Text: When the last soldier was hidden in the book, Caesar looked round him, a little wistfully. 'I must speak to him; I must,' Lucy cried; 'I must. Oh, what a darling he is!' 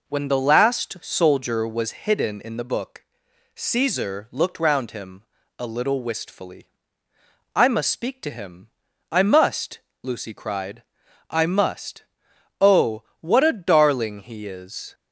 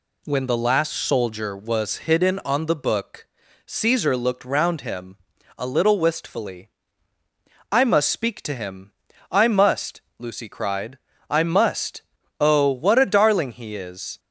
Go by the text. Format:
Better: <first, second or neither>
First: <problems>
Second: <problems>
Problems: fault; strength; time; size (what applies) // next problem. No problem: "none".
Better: first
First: none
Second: says "on" for "in"; at 2.4 s